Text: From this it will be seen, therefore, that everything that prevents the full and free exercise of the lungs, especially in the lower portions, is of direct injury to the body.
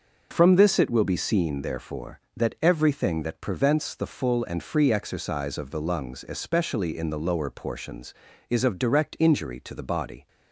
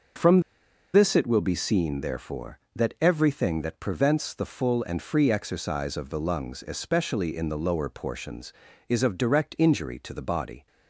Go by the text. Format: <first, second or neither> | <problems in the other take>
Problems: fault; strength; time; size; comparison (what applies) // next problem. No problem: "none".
first | pauses between "From" and "this"; noticeable; at 0.4 s; 0.53 s long